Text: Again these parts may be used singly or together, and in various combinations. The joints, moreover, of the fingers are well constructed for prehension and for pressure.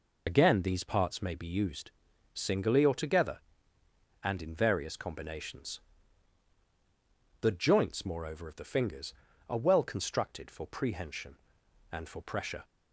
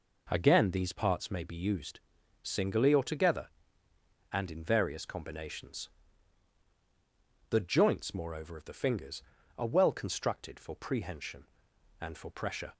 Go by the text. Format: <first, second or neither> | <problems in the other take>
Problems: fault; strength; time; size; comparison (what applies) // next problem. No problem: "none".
second | loses the start of "Again"; at 0.2 s; 90 ms // pauses between "used" and "singly"; at 1.9 s; 0.42 s long; also in the second